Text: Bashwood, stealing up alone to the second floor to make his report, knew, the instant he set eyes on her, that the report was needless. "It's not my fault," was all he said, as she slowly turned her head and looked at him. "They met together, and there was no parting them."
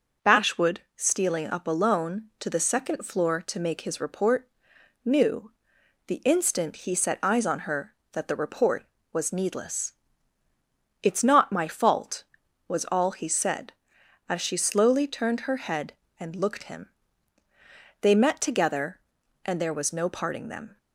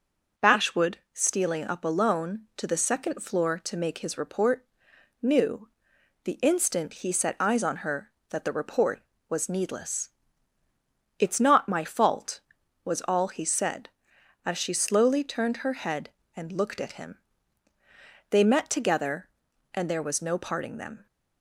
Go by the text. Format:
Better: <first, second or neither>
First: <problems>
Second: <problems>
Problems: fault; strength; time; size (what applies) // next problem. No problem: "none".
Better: second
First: skips "at"; at 16.6 s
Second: none